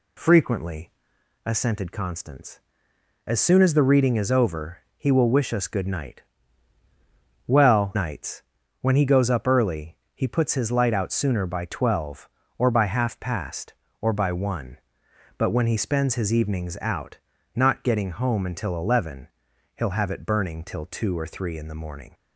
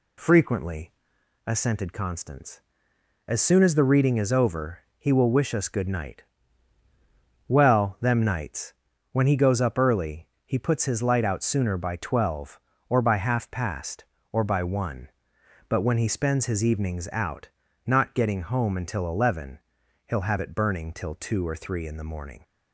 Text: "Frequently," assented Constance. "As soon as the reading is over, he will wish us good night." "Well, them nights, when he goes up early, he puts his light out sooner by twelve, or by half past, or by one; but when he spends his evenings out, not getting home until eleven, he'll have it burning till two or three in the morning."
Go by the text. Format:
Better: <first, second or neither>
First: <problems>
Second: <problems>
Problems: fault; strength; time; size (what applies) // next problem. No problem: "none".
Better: second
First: skips "them"; at 7.9 s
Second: none